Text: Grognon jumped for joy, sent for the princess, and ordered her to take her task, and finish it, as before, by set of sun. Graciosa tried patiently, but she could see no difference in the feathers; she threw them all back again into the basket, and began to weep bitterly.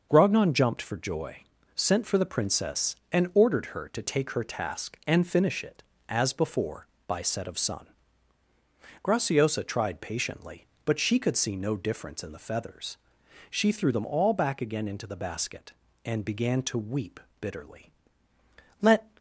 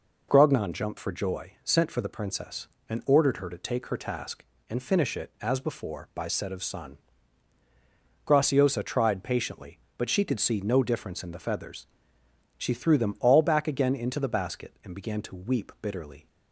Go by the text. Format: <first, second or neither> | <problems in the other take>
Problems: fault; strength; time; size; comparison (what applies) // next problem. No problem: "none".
second | pauses between "weep" and "bitterly"; slight; at 17.2 s; 0.18 s long // goes on to say "Let"; slight; from 18.8 s on; 0.30 s long